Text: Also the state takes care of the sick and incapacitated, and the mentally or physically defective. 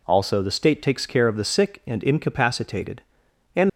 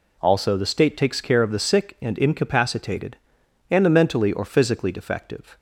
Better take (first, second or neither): second